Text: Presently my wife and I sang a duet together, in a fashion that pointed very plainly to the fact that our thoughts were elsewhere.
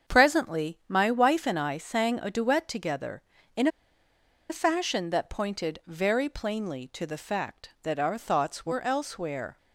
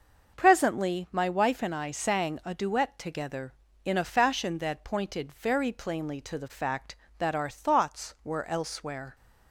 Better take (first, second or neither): second